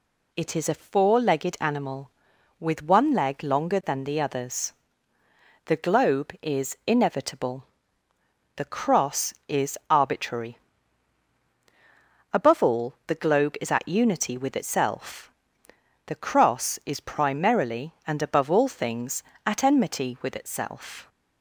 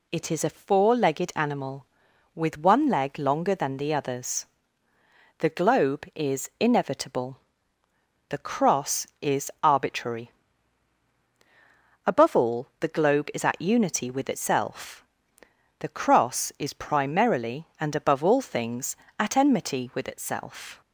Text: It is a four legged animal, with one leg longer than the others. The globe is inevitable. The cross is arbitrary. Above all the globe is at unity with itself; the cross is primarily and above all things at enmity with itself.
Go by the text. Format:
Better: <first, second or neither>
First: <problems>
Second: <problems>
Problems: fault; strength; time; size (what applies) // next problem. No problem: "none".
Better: neither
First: none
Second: none